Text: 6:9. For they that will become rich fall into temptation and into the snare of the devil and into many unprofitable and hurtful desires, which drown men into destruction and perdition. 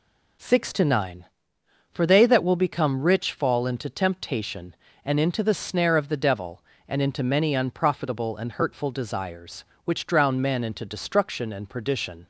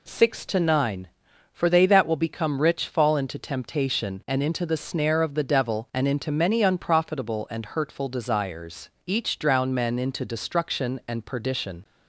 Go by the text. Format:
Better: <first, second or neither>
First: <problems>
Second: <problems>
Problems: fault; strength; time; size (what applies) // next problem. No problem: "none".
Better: first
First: none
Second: says "each" for "which"; at 9.0 s